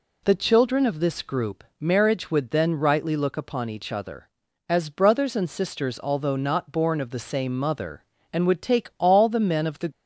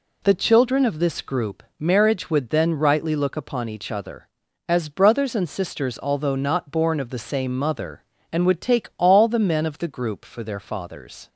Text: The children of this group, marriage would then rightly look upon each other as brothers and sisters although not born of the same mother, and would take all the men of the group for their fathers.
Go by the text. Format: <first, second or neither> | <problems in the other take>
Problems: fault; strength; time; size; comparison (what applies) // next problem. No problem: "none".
second | stops before "group for their fathers"; at 9.9 s